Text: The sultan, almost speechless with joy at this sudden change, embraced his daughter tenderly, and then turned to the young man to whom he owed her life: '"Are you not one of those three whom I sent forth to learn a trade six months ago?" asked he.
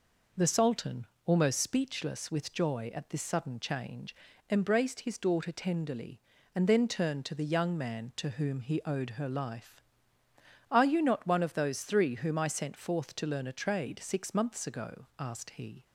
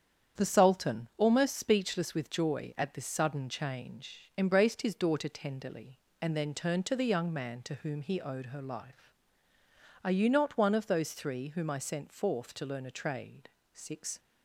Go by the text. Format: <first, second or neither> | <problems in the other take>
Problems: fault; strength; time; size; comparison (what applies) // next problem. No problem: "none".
first | starts louder than the rest; strong; until 1.4 s; 8.5 dB // pauses between "trade" and "six"; slight; at 13.4 s; 0.24 s long // stops before "months ago asked he"; at 14.1 s